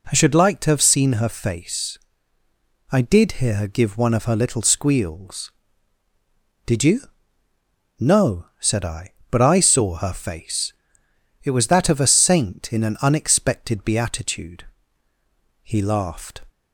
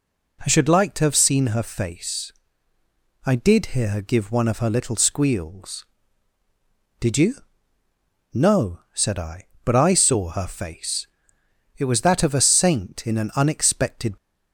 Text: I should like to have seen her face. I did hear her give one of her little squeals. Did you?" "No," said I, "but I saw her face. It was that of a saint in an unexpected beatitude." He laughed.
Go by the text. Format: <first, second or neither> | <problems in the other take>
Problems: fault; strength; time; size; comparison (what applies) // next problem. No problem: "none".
first | stops before "beatitude He laughed"; at 14.1 s